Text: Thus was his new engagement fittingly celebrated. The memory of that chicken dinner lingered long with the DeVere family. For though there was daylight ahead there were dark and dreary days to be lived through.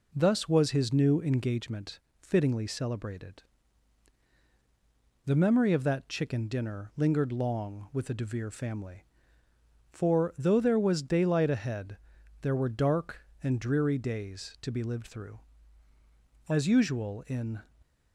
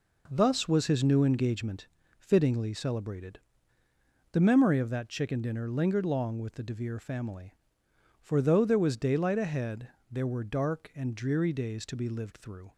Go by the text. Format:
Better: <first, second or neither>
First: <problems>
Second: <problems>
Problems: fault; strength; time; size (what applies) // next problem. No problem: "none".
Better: second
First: pauses between "engagement" and "fittingly"; slight; at 1.9 s; 0.22 s long // pauses between "ahead" and "there"; noticeable; at 11.9 s; 0.46 s long // goes on to say "As usual in"; noticeable; from 16.4 s on; 1.1 s long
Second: pauses between "engagement" and "fittingly"; slight; at 1.8 s; 0.32 s long // pauses between "ahead" and "there"; slight; at 9.8 s; 0.22 s long